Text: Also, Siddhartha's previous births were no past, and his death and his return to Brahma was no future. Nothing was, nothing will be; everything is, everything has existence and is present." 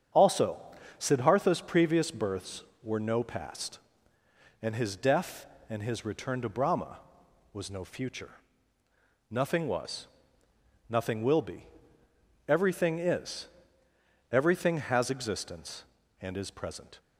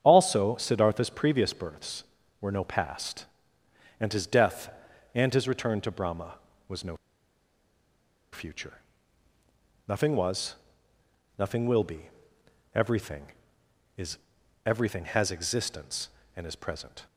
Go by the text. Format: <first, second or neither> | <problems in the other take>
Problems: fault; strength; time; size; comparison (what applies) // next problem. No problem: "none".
first | starts louder than the rest; strong; until 1.0 s; 8 dB; strong in the first // pauses between "no" and "future"; strong; at 6.9 s; 1.3 s long